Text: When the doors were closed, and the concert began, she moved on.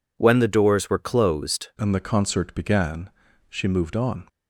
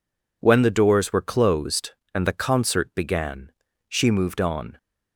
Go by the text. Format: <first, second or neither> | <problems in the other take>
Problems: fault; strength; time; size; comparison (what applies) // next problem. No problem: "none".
second | changes voice at "and"; from 1.7 s on; 2.5 s long